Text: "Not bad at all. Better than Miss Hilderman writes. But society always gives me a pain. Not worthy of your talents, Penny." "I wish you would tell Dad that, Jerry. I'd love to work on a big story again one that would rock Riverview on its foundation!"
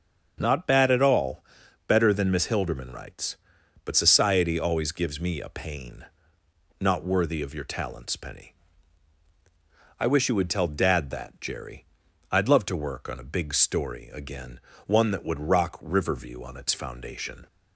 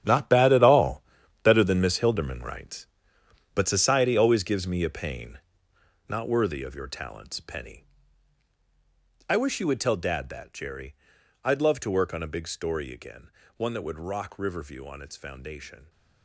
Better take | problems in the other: first | gets quieter; strong; throughout; 12.5 dB // starts louder than the rest; strong; until 1.4 s; 9.5 dB; also in the first // pauses between "again" and "one"; slight; at 13.3 s; 0.26 s long; slight in the first

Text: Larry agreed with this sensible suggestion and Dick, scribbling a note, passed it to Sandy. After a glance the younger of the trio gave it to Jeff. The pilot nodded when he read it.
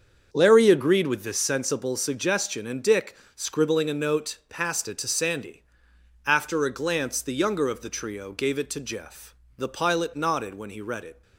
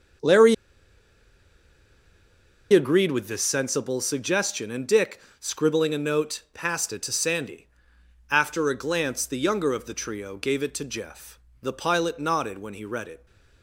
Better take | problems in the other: first | starts louder than the rest; until 3.4 s; 6.5 dB; also in the first // pauses between "Larry" and "agreed"; strong; at 0.5 s; 2.1 s long

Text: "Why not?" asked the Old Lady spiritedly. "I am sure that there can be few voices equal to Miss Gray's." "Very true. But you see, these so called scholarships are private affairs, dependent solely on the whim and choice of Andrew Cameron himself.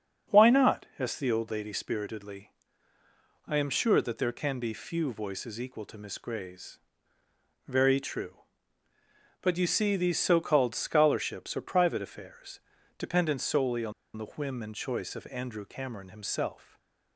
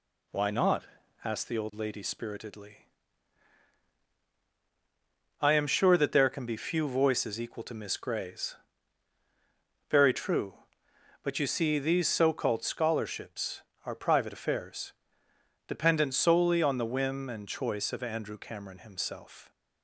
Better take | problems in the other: second | starts louder than the rest; until 1.4 s; 6.5 dB // pauses between "on" and "the"; slight; at 13.9 s; 0.24 s long // stays silent after the last word; slight; from 16.5 s on; 0.6 s long

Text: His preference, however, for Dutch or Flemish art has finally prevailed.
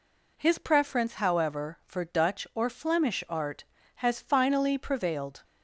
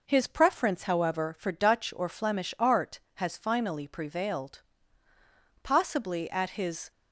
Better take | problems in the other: first | goes on to say "Possibly at his"; noticeable; from 5.6 s on; 1.2 s long

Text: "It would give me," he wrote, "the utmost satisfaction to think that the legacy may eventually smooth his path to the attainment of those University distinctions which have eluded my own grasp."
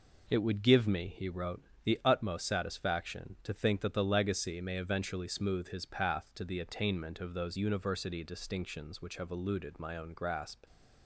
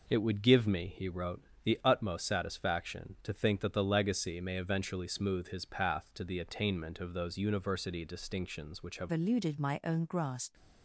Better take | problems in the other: first | changes voice at "eluded"; from 9.1 s on; 1.4 s long

